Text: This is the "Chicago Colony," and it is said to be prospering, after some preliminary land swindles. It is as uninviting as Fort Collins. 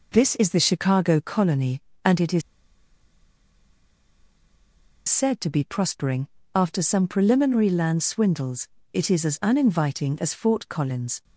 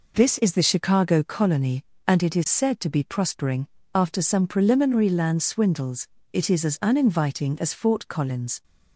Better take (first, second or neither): second